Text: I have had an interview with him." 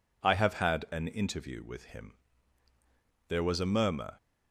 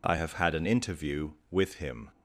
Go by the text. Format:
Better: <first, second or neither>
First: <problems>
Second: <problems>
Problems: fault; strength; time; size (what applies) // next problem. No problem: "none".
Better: second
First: goes on to say "There was a murmur"; noticeable; from 3.2 s on; 0.88 s long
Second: none